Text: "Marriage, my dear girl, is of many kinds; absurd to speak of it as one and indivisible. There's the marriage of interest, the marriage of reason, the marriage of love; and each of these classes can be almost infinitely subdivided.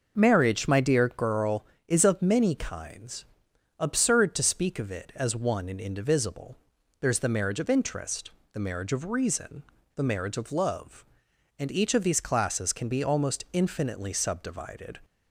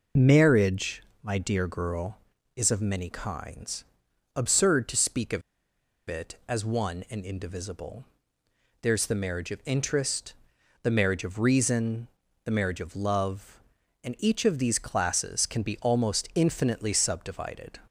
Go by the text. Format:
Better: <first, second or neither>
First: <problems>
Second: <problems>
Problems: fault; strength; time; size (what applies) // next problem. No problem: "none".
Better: first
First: none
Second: pauses between "of" and "it"; noticeable; at 5.4 s; 0.68 s long